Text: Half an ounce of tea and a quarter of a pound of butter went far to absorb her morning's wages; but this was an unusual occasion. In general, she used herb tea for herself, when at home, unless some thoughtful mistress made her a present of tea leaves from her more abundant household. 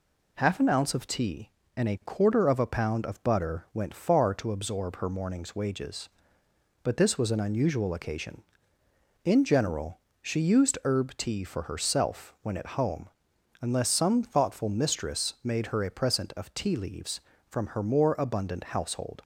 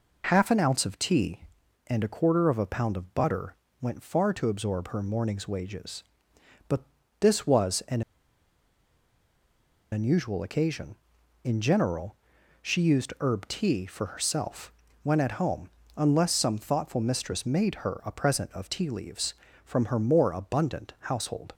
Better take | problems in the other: first | pauses between "butter" and "went"; slight; at 3.5 s; 0.26 s long // pauses between "but" and "this"; at 6.8 s; 0.38 s long // pauses between "an" and "unusual"; strong; at 8.0 s; 1.9 s long

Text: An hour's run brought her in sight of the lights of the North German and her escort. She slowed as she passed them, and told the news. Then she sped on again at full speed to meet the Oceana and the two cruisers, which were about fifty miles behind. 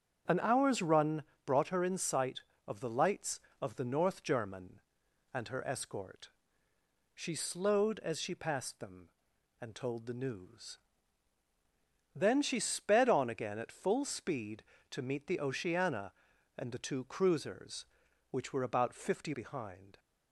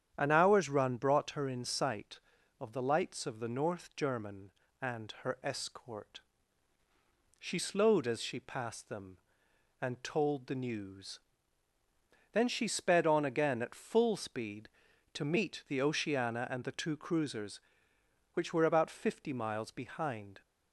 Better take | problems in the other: second | starts louder than the rest; strong; until 1.5 s; 7.5 dB; strong in the second // pauses between "run" and "brought"; slight; at 1.2 s; 0.22 s long // skips "miles"; at 19.3 s

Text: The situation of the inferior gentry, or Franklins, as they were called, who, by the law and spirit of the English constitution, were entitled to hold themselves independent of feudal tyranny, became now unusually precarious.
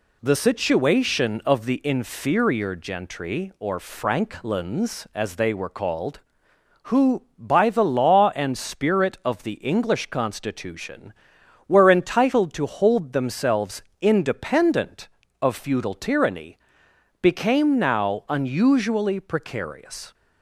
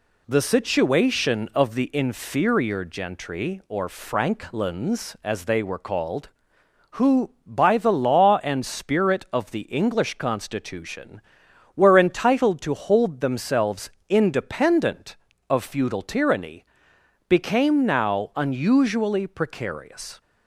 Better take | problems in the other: neither | pauses between "themselves" and "independent"; slight; the same in both

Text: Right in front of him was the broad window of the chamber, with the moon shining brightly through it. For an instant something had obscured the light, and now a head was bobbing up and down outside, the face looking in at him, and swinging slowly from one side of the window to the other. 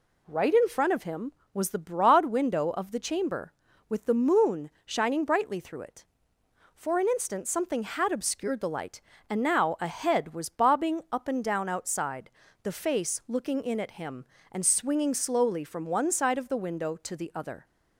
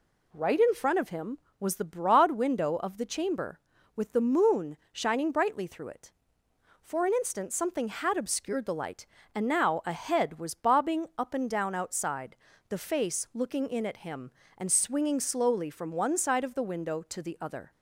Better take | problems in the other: neither | pauses between "moon" and "shining"; slight; the same in both

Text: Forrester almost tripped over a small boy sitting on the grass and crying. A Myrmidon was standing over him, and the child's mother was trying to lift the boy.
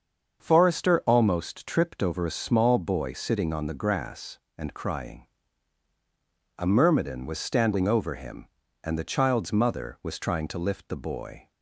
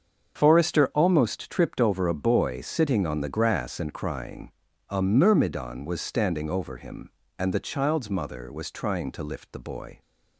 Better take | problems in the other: first | starts louder than the rest; until 1.3 s; 7 dB; also in the first // skips "small"; at 2.2 s

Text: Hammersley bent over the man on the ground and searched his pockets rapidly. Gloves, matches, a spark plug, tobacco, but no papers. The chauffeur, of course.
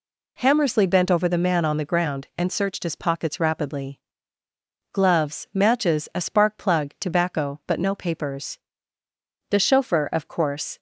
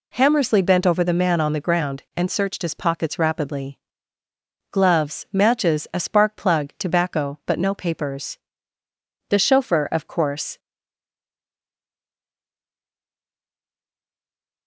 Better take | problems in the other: first | stays silent after the last word; strong; from 10.5 s on; 4.1 s long

